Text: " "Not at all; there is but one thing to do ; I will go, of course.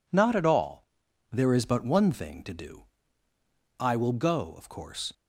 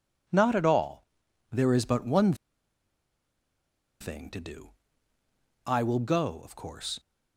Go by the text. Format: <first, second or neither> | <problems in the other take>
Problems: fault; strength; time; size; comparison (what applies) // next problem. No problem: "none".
first | pauses between "one" and "thing"; strong; at 2.3 s; 1.6 s long